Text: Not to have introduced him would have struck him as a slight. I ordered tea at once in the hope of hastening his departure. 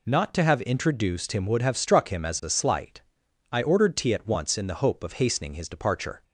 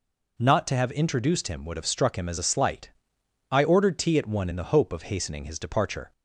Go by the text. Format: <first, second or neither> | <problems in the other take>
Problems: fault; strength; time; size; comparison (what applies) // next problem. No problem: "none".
first | says "one" for "once"; at 4.2 s